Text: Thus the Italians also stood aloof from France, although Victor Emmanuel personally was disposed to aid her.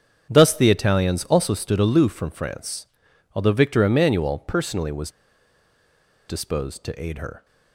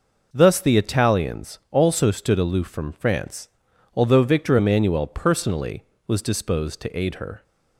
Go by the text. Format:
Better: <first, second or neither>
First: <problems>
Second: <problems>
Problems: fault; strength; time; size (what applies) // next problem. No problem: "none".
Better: second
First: starts louder than the rest; strong; until 1.3 s; 7.5 dB // pauses between "was" and "disposed"; at 5.0 s; 1.1 s long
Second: none